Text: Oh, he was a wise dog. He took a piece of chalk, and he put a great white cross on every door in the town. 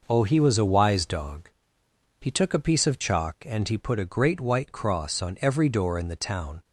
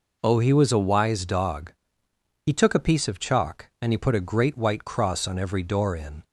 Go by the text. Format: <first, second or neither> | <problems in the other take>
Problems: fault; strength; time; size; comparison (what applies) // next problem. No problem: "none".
first | stops before "the town"; at 6.2 s